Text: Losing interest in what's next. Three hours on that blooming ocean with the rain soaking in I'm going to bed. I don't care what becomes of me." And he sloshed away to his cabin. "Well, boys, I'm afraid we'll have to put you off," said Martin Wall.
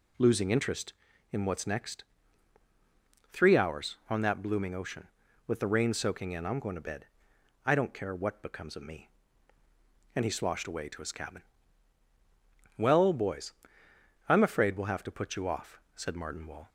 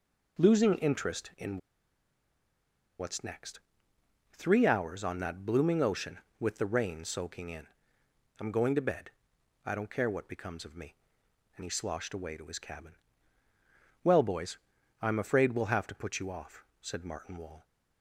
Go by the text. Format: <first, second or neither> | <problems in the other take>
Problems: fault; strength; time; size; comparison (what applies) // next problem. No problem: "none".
first | pauses between "in" and "what's"; strong; at 1.5 s; 1.4 s long // pauses between "in" and "I'm"; noticeable; at 7.6 s; 0.74 s long